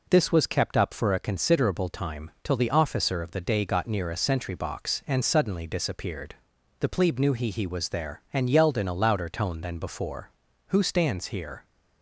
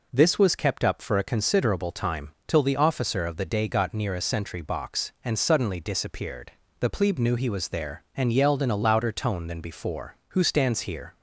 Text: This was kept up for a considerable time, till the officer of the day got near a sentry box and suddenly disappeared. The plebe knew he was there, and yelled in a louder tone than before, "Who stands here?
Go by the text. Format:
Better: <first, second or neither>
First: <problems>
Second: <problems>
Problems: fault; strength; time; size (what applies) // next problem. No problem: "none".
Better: second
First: says "he" twice; at 7.5 s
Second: none